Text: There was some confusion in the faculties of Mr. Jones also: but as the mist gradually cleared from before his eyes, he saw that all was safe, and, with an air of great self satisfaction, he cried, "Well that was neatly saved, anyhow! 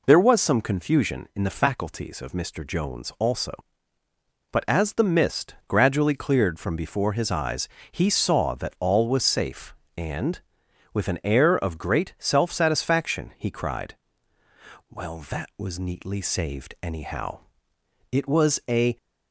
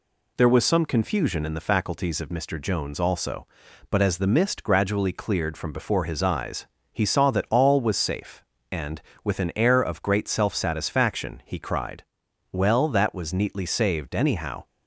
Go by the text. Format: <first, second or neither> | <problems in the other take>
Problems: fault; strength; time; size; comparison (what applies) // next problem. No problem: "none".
second | goes on to say "it was a"; noticeable; from 18.1 s on; 0.84 s long